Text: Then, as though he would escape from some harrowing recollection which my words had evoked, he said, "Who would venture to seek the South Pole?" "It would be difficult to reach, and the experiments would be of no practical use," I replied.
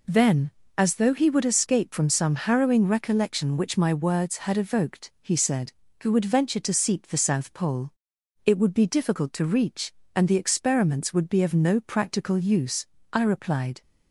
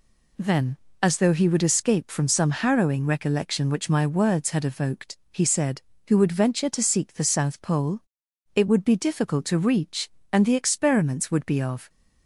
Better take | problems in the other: first | stops before "no practical use I replied"; at 11.8 s

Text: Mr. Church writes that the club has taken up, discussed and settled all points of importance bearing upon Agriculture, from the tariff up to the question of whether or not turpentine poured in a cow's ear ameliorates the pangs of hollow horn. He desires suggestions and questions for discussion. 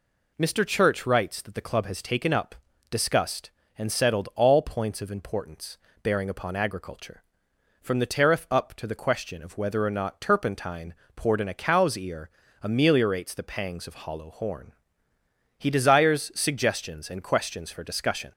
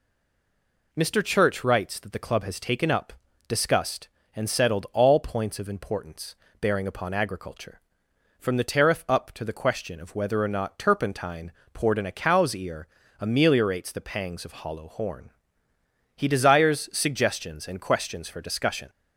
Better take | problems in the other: first | stays silent before the first word; slight; until 0.9 s; 0.9 s long // pauses between "importance" and "bearing"; slight; at 6.3 s; 0.24 s long; slight in the first // pauses between "turpentine" and "poured"; slight; at 11.5 s; 0.20 s long; slight in the first // pauses between "ear" and "ameliorates"; slight; at 12.8 s; 0.32 s long; slight in the first

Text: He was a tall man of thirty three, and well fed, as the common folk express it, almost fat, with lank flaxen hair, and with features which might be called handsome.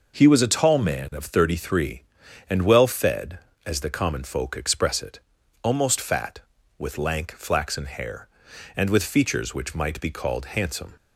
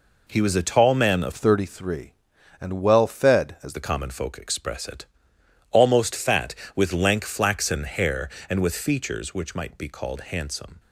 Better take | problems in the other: first | changes voice from "thirty" to "as"; from 1.3 to 3.7 s; 2.4 s long

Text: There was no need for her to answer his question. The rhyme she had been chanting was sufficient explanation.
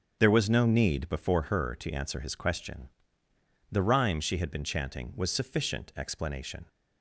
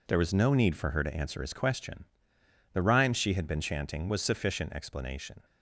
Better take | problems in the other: second | starts louder than the rest; strong; until 1.2 s; 7.5 dB // says "before" for "for"; at 1.0 s

